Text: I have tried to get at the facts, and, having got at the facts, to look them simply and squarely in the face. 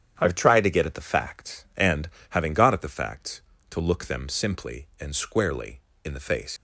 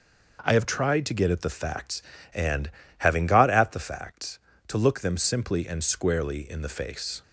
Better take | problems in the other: second | starts louder than the rest; strong; until 1.1 s; 9.5 dB // leaves "face" unfinished; at 6.5 s; 100 ms

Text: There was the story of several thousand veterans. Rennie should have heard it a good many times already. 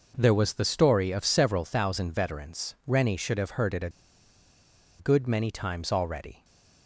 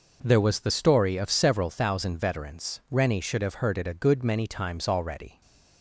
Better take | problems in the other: second | pauses between "a" and "good"; at 3.9 s; 1.0 s long // stays silent after the last word; slight; from 6.3 s on; 0.5 s long; slight in the second

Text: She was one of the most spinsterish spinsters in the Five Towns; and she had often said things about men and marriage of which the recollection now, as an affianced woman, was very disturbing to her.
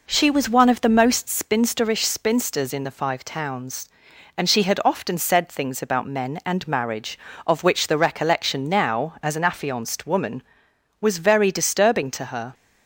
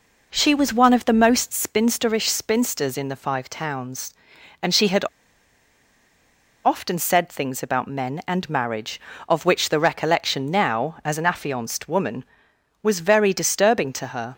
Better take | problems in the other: first | pauses between "had" and "often"; strong; at 5.0 s; 1.6 s long

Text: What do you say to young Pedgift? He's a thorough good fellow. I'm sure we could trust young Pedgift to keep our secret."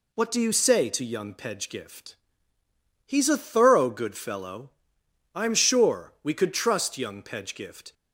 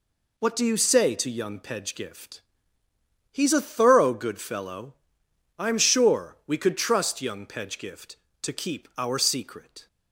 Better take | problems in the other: second | stops before "to keep our secret"; at 7.9 s

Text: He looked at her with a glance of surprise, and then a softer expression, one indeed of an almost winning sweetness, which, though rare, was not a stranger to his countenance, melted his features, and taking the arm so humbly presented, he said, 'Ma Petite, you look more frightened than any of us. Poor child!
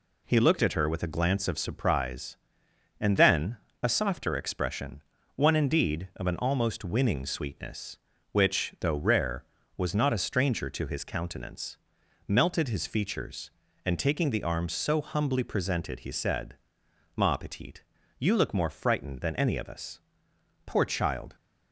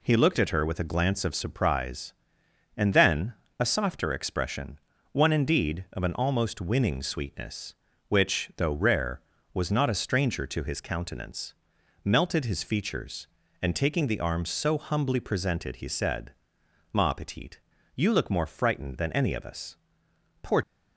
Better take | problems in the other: first | pauses between "then" and "a"; slight; at 3.3 s; 0.26 s long; slight in the first // stops before "child"; at 20.6 s

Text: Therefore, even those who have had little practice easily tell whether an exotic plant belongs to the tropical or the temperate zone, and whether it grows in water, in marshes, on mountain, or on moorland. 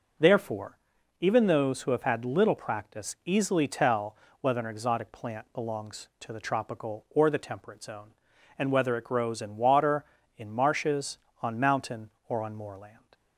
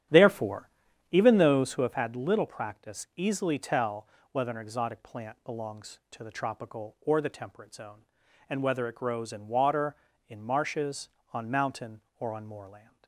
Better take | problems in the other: first | starts louder than the rest; strong; until 2.0 s; 11 dB // pauses between "tell" and "whether"; slight; at 4.0 s; 0.26 s long; slight in the first

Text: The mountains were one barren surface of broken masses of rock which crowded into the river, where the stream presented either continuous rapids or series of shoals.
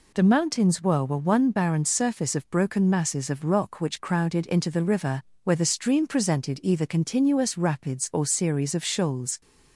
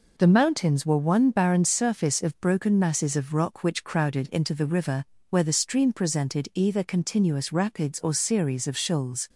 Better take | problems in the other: second | says "were" twice; at 1.0 s

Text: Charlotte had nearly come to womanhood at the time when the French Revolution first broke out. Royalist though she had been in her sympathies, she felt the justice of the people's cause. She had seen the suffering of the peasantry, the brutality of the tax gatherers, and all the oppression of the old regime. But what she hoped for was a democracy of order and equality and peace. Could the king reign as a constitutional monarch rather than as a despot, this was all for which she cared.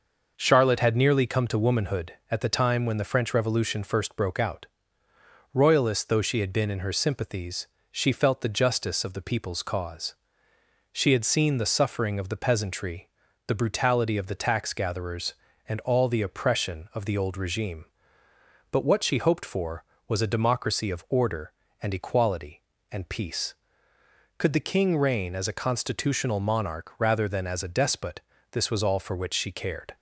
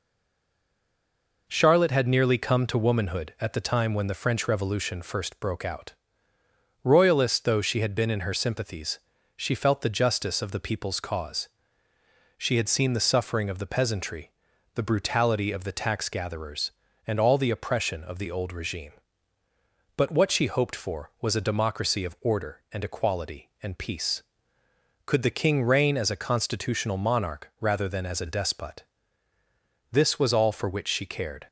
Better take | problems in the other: first | stays silent before the first word; noticeable; until 1.4 s; 1.4 s long

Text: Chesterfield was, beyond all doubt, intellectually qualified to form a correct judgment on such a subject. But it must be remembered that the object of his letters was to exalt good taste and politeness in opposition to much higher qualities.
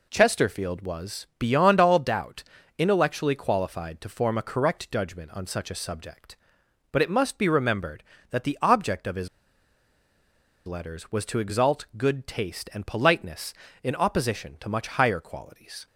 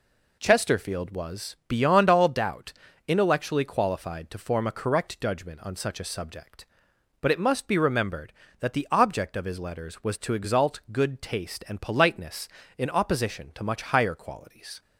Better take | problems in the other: second | pauses between "his" and "letters"; strong; at 9.2 s; 1.3 s long

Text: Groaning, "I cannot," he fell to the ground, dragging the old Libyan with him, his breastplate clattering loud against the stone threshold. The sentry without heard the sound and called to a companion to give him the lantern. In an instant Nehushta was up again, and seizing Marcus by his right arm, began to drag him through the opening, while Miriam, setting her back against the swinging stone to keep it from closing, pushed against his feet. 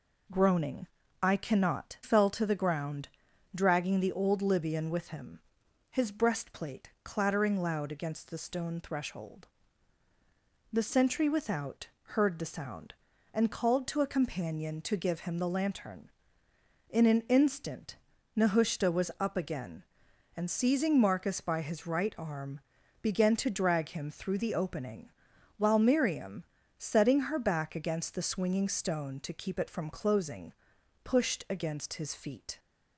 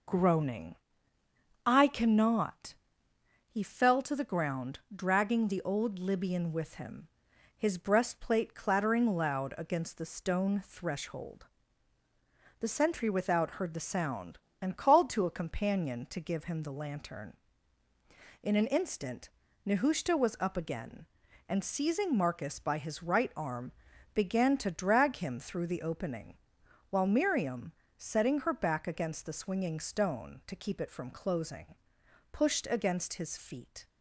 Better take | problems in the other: second | skips "he"; at 2.0 s // pauses between "without" and "heard"; slight; at 11.8 s; 0.28 s long // pauses between "instant" and "Nehushta"; at 17.9 s; 0.38 s long; also in the second

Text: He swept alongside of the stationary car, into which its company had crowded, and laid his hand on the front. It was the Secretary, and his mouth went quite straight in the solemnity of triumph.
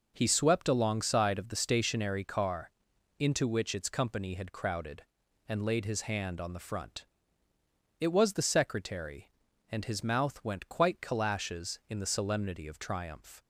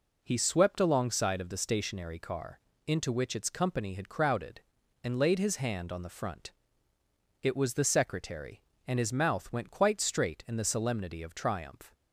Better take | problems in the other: second | says "calashes" for "straight"; at 11.0 s

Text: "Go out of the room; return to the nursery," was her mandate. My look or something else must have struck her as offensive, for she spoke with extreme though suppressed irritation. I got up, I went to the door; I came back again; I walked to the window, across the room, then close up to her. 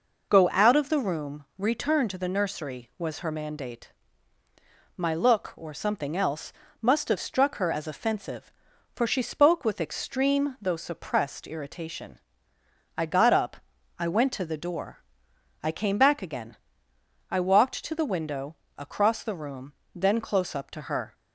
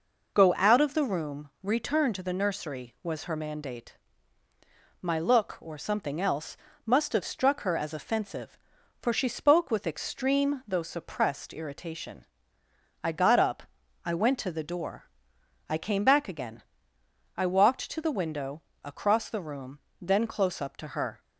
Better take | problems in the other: neither | pauses between "else" and "must"; slight; the same in both

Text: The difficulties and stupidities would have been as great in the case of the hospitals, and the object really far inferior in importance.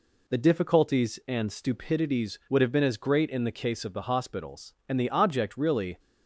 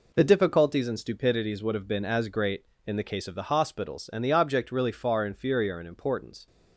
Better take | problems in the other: second | stops before "far inferior in importance"; at 5.9 s

